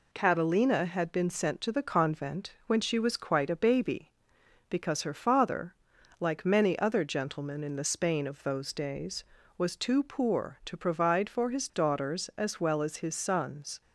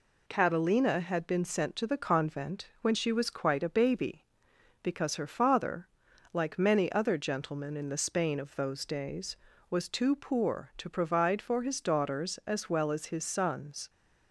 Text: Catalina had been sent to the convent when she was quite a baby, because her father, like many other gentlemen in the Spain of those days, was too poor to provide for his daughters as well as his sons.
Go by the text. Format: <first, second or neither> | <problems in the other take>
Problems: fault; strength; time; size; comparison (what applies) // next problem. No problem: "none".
neither | none